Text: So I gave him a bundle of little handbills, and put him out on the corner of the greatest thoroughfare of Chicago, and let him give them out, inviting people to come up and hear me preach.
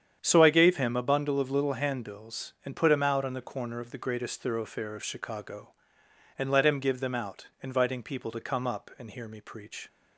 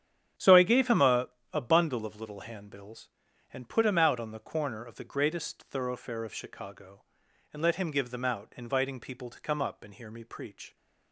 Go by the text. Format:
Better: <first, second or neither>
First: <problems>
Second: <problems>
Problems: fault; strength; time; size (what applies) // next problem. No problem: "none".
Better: first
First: starts louder than the rest; strong; until 1.2 s; 8.5 dB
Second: starts louder than the rest; strong; until 1.6 s; 9.5 dB // says "a" twice; at 1.5 s